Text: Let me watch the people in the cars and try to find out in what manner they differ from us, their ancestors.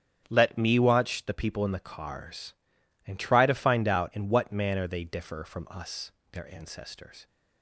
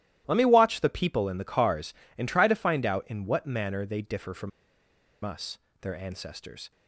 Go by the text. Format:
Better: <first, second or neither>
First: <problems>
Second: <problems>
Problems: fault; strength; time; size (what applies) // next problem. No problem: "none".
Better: first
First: starts louder than the rest; strong; until 1.3 s; 8.5 dB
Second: starts louder than the rest; strong; until 1.2 s; 14 dB // pauses between "from" and "us"; noticeable; at 4.5 s; 0.74 s long